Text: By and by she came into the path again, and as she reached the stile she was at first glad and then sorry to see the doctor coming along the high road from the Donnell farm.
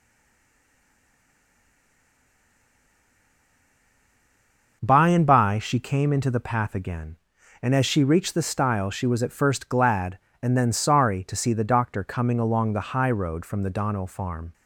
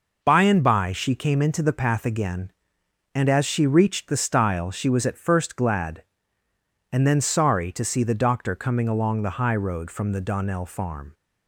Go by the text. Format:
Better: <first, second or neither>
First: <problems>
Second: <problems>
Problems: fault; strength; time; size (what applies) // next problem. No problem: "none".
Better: second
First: stays silent before the first word; strong; until 4.8 s; 4.8 s long // starts louder than the rest; noticeable; until 5.8 s; 6 dB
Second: none